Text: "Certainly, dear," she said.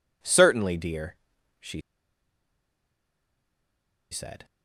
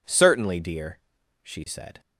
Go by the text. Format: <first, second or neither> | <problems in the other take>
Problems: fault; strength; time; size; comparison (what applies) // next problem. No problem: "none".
second | pauses between "she" and "said"; strong; at 1.8 s; 2.3 s long